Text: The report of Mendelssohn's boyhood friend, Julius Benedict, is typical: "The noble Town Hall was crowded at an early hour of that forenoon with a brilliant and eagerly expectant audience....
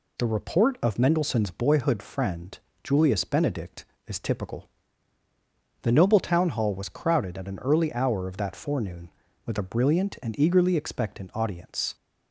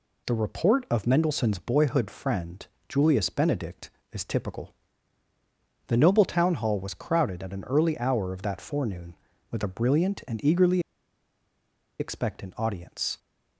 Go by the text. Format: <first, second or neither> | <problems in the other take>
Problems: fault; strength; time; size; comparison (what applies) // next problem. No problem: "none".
first | pauses between "eagerly" and "expectant"; at 10.8 s; 1.1 s long